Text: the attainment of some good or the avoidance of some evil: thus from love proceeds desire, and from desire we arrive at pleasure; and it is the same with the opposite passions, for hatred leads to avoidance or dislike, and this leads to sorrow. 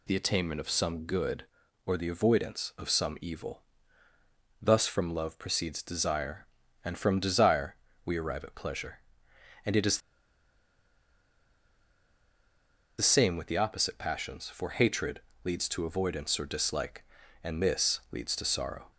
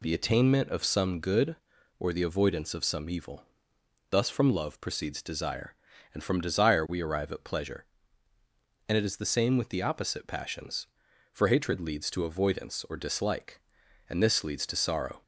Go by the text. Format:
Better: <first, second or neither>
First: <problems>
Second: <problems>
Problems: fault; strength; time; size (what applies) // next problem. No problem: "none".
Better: second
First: pauses between "desire" and "we"; slight; at 7.7 s; 0.30 s long // pauses between "is" and "the"; strong; at 9.9 s; 3.0 s long // pauses between "hatred" and "leads"; slight; at 15.2 s; 0.22 s long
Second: none